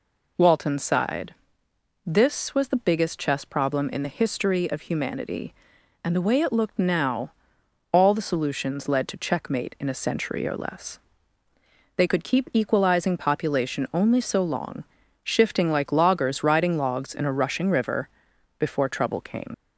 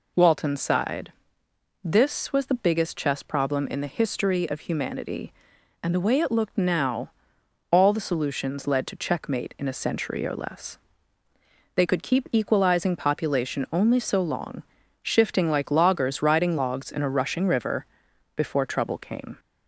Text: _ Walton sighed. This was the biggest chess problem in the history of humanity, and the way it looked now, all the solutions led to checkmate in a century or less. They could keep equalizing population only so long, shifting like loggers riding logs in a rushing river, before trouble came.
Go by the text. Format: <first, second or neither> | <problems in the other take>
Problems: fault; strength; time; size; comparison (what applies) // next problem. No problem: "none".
second | leaves "came" unfinished; at 19.5 s; 75 ms